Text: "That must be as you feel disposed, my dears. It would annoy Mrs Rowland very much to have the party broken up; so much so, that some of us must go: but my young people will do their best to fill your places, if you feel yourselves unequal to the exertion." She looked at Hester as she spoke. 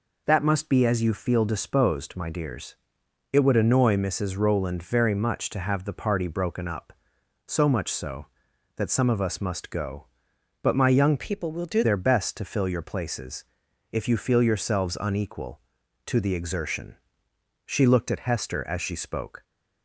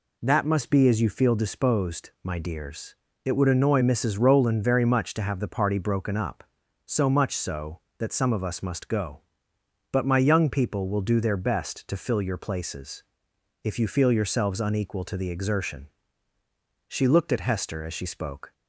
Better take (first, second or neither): second